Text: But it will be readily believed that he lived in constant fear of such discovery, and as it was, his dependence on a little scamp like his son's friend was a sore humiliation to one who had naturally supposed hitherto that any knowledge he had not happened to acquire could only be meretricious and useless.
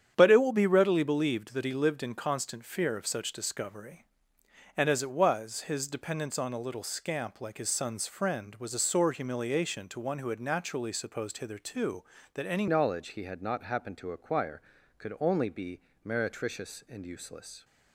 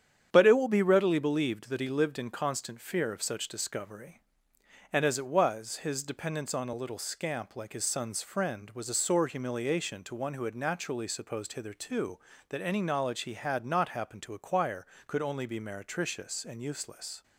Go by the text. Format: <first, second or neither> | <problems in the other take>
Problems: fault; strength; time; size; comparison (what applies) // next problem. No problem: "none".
second | starts louder than the rest; strong; until 1.1 s; 9 dB; strong in the second // changes voice at "knowledge"; from 12.6 s on; 5.0 s long // pauses between "be" and "meretricious"; slight; at 15.7 s; 0.24 s long